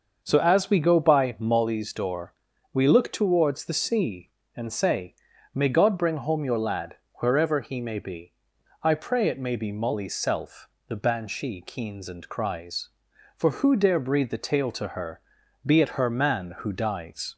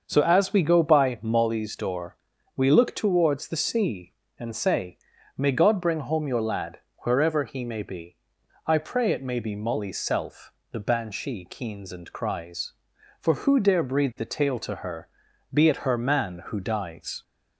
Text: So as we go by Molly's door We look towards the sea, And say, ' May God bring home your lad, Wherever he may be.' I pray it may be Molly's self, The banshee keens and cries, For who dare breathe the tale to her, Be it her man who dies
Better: neither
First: starts louder than the rest; until 1.2 s; 6.5 dB // pauses between "door" and "We"; at 2.3 s; 0.40 s long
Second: starts louder than the rest; until 1.0 s; 6.5 dB // pauses between "door" and "We"; at 2.1 s; 0.40 s long

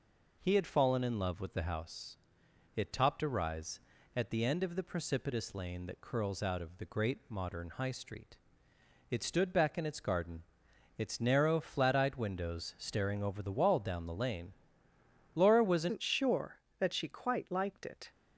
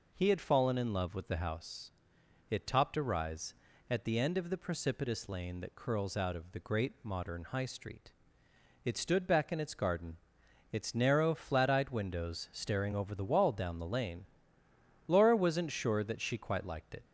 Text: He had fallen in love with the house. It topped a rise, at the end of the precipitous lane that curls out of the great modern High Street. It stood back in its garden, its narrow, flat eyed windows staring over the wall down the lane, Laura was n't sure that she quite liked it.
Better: second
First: changes voice at "n't"; from 15.9 s on; 2.1 s long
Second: none

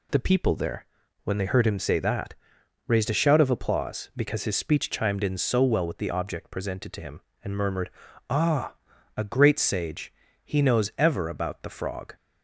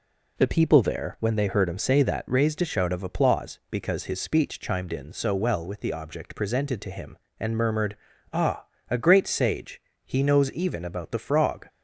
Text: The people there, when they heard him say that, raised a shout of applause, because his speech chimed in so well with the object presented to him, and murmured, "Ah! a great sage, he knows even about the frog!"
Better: second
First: says "ever" for "even"; at 10.9 s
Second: none

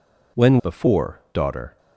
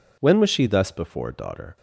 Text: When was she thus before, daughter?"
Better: second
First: skips "was she thus"; at 0.5 s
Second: none

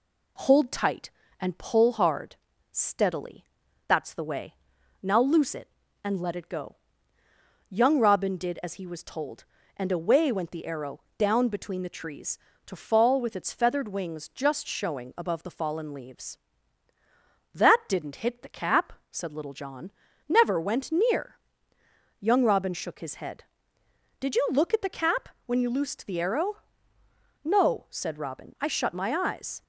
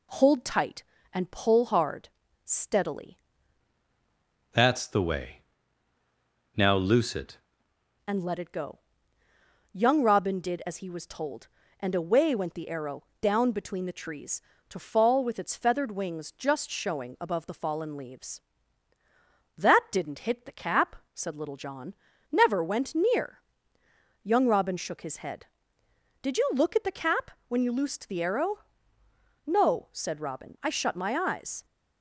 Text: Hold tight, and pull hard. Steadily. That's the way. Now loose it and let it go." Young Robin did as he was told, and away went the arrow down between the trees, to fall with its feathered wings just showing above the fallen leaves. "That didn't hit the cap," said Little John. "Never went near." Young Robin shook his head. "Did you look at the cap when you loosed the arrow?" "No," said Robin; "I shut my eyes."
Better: first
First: pauses between "arrow" and "down"; slight; at 10.9 s; 0.18 s long // pauses between "cap" and "when"; slight; at 25.2 s; 0.18 s long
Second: changes voice from "That's" to "it"; from 4.5 to 7.3 s; 2.8 s long // pauses between "arrow" and "down"; slight; at 13.0 s; 0.18 s long // pauses between "cap" and "when"; slight; at 27.3 s; 0.18 s long

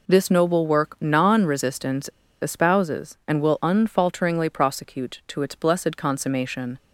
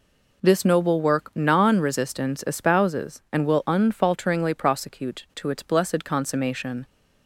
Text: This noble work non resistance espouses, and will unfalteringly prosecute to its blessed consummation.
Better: second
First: pauses between "resistance" and "espouses"; slight; at 2.0 s; 0.33 s long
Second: none

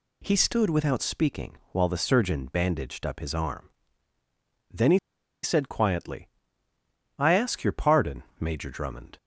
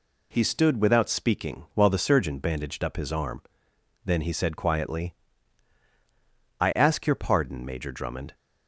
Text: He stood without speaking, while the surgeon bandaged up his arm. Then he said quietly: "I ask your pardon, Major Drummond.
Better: second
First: pauses between "he" and "said"; at 4.9 s; 0.44 s long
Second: none

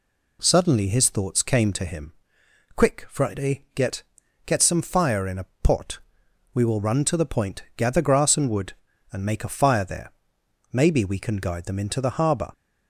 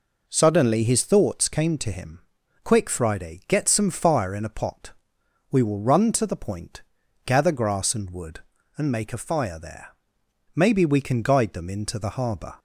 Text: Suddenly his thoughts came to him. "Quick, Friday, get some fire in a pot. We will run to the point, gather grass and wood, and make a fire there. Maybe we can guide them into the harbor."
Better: second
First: says "get" twice; at 4.4 s // pauses between "a" and "pot"; slight; at 5.4 s; 0.18 s long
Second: none

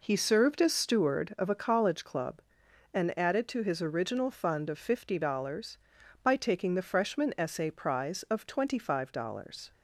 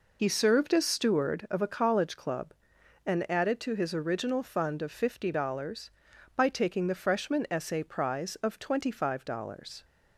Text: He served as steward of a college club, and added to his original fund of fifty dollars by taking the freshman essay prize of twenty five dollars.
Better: first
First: none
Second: loses the start of "He"; at 0.1 s; 50 ms

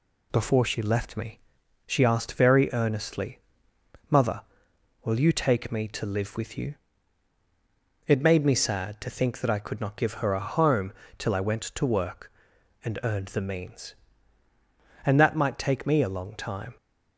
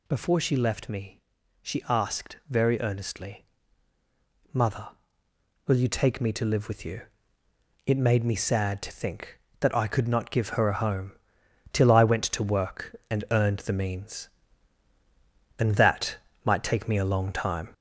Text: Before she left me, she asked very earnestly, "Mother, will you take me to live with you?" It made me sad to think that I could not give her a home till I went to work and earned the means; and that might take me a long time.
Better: first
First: pauses between "home" and "till"; slight; at 10.9 s; 0.24 s long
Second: gets louder; throughout; 3.5 dB // pauses between "home" and "till"; noticeable; at 11.1 s; 0.58 s long // pauses between "that" and "might"; slight; at 16.1 s; 0.26 s long

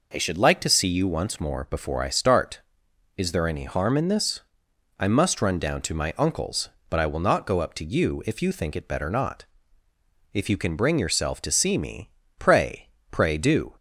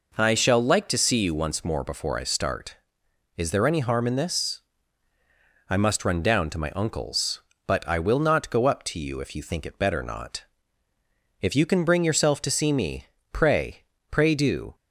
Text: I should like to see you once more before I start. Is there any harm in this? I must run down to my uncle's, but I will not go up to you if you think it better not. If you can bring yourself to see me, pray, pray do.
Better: first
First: none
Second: says "shall" for "should"; at 0.3 s

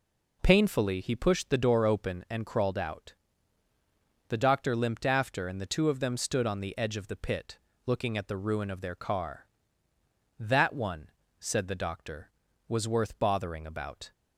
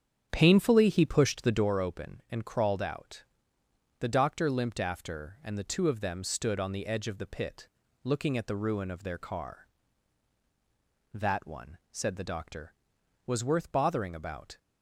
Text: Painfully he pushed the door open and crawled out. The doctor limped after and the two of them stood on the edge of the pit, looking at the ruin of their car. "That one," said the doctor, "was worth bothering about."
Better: first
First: none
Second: starts louder than the rest; strong; until 1.7 s; 8 dB

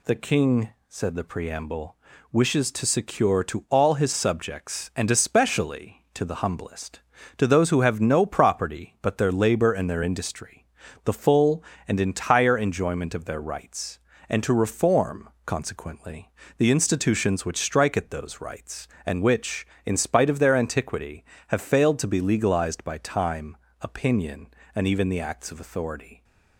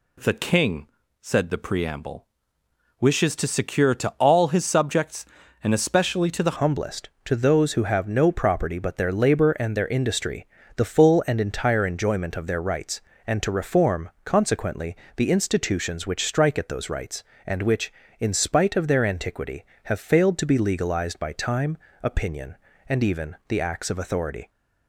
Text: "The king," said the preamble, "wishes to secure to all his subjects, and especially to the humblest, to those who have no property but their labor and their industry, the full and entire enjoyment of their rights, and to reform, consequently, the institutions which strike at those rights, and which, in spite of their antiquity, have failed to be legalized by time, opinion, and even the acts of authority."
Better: first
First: none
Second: changes voice at "humblest"; from 6.5 s on; 17.9 s long

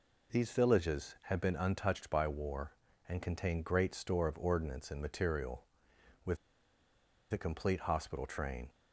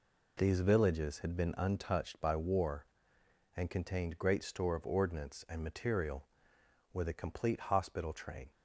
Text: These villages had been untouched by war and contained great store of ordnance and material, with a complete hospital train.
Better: second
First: pauses between "with" and "a"; noticeable; at 6.3 s; 0.95 s long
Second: none

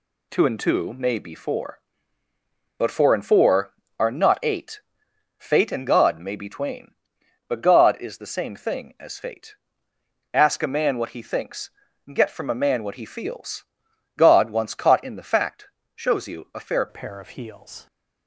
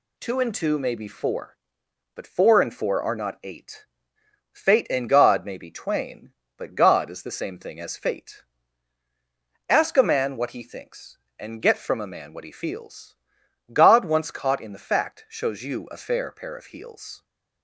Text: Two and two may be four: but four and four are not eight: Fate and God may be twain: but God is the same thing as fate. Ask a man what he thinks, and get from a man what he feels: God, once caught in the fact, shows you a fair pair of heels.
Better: second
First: changes voice at "pair"; from 16.8 s on; 1.0 s long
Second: none

